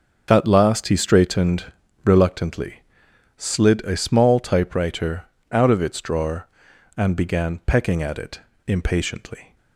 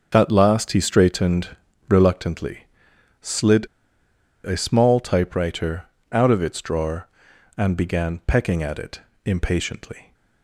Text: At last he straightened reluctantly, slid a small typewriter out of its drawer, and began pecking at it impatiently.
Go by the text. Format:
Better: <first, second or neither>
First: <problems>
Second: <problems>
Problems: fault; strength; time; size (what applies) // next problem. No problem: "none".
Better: first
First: starts louder than the rest; until 1.3 s; 6 dB // pauses between "straightened" and "reluctantly"; at 1.6 s; 0.40 s long // pauses between "typewriter" and "out"; slight; at 5.2 s; 0.26 s long // pauses between "it" and "impatiently"; slight; at 8.3 s; 0.26 s long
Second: starts louder than the rest; until 1.1 s; 6.5 dB // pauses between "straightened" and "reluctantly"; at 1.4 s; 0.40 s long // pauses between "slid" and "a"; noticeable; at 3.6 s; 0.78 s long // pauses between "typewriter" and "out"; slight; at 5.8 s; 0.26 s long // pauses between "it" and "impatiently"; slight; at 8.9 s; 0.24 s long